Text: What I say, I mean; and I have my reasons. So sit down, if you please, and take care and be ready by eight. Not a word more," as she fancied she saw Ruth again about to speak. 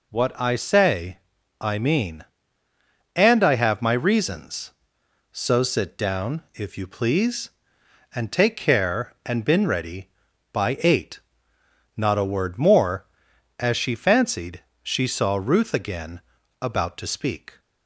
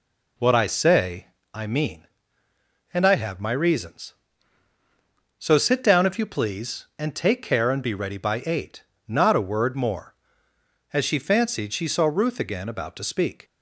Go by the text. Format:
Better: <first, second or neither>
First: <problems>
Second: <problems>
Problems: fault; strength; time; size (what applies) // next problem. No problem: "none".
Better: second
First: says "been" for "be"; at 9.4 s // pauses between "fancied" and "she"; slight; at 14.6 s; 0.18 s long // pauses between "again" and "about"; at 16.2 s; 0.38 s long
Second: none